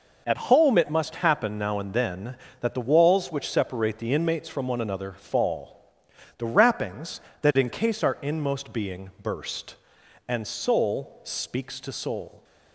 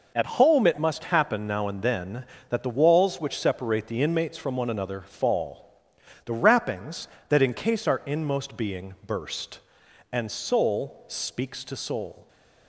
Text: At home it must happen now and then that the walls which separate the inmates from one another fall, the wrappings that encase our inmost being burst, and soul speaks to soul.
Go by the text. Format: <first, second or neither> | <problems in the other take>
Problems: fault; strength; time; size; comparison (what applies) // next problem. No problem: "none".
neither | none